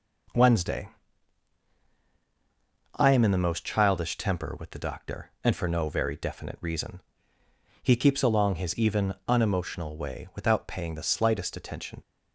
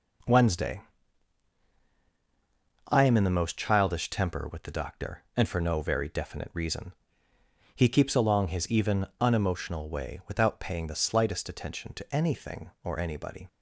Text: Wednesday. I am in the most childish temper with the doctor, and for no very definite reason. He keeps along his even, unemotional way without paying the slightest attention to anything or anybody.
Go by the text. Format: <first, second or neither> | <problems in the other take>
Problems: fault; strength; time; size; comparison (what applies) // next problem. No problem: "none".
second | stops before "to anything or anybody"; at 12.0 s